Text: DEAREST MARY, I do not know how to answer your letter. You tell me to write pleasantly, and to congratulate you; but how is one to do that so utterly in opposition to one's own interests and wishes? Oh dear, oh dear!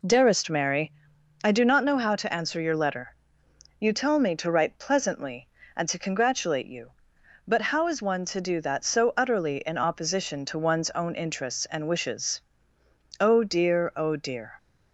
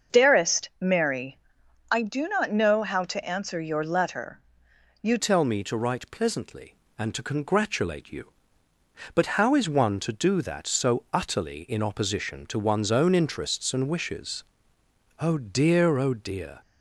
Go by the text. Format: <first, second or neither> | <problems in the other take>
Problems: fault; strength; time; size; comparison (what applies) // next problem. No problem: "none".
first | starts louder than the rest; until 1.2 s; 6.5 dB // changes voice at "tell"; from 5.1 s on; 11.4 s long